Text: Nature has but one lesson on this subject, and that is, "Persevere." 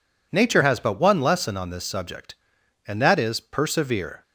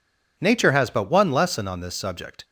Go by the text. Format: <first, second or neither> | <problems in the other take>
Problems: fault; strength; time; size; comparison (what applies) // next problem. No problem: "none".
first | stops before "and that is Persevere"; at 2.4 s